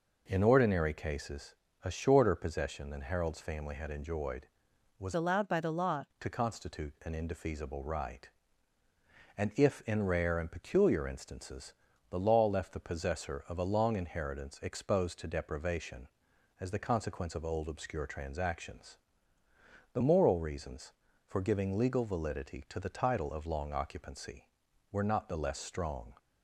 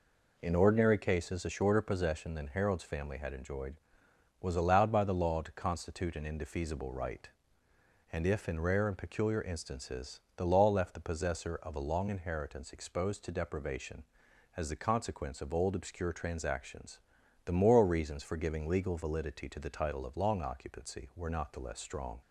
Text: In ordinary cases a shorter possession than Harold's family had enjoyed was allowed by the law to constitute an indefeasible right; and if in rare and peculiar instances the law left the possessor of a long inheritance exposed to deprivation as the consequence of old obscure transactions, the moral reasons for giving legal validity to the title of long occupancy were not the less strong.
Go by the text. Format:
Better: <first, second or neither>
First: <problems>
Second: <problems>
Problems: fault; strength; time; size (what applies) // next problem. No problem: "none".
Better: second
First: pauses between "cases" and "a"; slight; at 1.5 s; 0.30 s long // changes voice from "allowed" to "law"; from 5.1 to 6.0 s; 0.9 s long // pauses between "instances" and "the"; at 11.7 s; 0.38 s long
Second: pauses between "instances" and "the"; slight; at 10.1 s; 0.16 s long